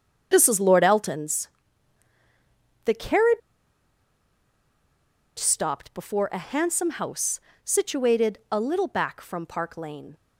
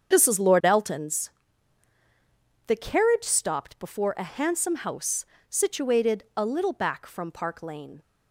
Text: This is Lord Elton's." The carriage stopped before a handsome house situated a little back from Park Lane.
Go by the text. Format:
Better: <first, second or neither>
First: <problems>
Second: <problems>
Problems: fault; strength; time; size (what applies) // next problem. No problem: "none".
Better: second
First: starts louder than the rest; strong; until 1.3 s; 7.5 dB // pauses between "carriage" and "stopped"; strong; at 3.4 s; 1.9 s long // pauses between "house" and "situated"; slight; at 7.3 s; 0.26 s long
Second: starts louder than the rest; strong; until 1.1 s; 7 dB // pauses between "house" and "situated"; slight; at 5.2 s; 0.26 s long